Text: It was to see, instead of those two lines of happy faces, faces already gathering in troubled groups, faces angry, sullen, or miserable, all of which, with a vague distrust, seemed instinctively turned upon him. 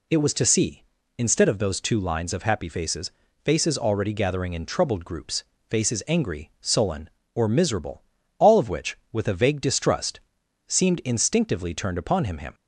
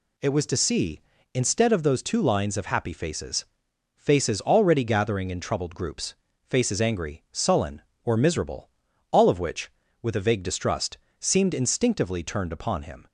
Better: second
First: says "him" twice; at 12.3 s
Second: none

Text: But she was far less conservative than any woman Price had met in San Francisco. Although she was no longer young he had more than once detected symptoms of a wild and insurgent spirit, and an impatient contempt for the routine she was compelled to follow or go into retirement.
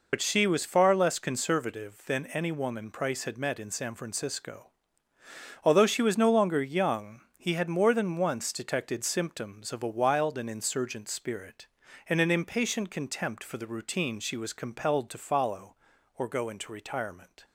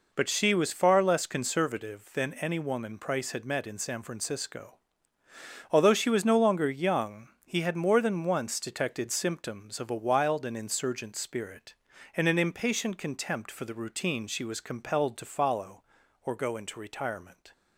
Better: second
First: loses the start of "But"; at 0.1 s; 65 ms // pauses between "young" and "he"; slight; at 7.2 s; 0.16 s long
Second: pauses between "young" and "he"; slight; at 7.2 s; 0.16 s long

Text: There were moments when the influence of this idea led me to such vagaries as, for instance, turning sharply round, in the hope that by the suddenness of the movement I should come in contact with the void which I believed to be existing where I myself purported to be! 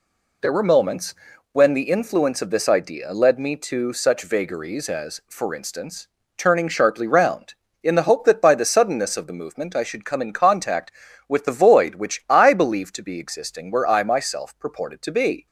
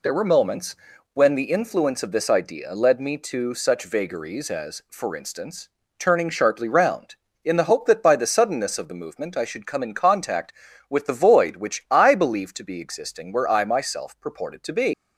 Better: first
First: pauses between "moments" and "when"; at 1.1 s; 0.38 s long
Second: pauses between "moments" and "when"; at 0.7 s; 0.38 s long // leaves "be" unfinished; at 14.9 s; 140 ms

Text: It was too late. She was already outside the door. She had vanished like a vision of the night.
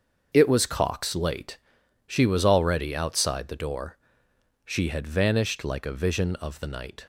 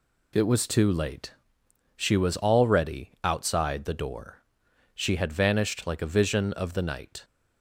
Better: second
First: starts louder than the rest; until 1.3 s; 6.5 dB // says "cox" for "too"; at 0.6 s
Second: none

